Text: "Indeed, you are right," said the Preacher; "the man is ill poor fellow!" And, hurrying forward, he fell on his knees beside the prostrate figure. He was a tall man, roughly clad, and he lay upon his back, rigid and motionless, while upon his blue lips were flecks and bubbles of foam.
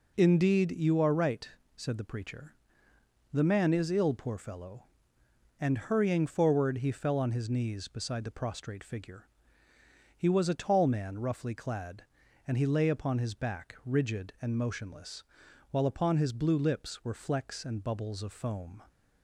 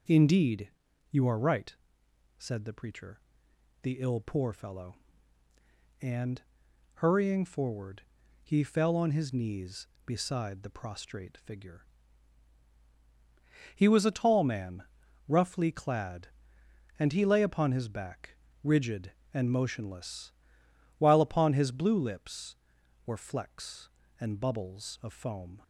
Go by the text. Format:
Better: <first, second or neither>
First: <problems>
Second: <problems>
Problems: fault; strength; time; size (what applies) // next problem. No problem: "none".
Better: first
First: none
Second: skips "man is"; at 3.9 s